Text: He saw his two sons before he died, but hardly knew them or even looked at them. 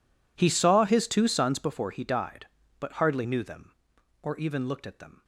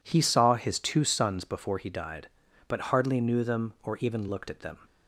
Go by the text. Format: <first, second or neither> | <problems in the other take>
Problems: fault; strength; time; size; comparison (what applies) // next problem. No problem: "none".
second | gets quieter; strong; throughout; 22.5 dB